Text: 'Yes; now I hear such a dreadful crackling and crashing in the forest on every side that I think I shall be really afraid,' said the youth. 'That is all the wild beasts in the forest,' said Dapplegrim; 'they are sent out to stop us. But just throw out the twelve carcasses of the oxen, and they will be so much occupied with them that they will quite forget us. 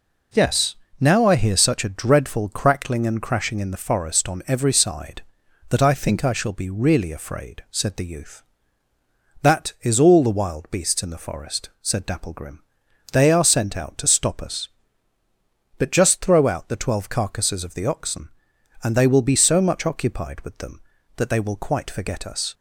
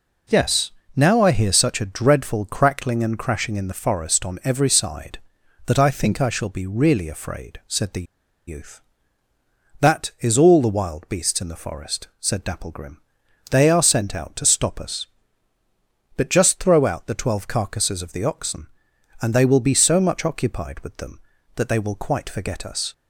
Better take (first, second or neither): first